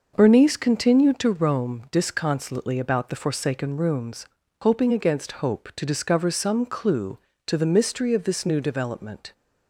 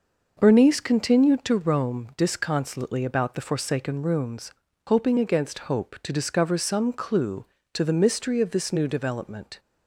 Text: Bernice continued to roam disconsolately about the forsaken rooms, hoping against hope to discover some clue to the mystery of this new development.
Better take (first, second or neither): neither